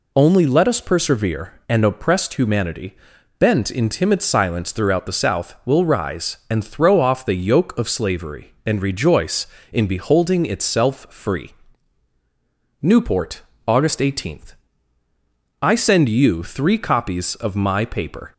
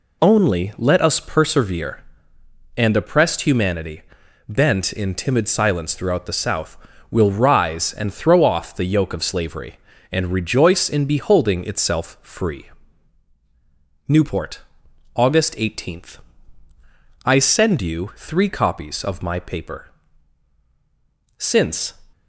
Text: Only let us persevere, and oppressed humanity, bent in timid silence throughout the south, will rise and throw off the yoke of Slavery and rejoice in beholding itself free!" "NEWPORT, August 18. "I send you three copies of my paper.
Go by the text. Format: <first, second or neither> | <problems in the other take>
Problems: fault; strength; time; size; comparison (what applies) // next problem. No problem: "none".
first | goes on to say "Since"; from 21.3 s on; 0.56 s long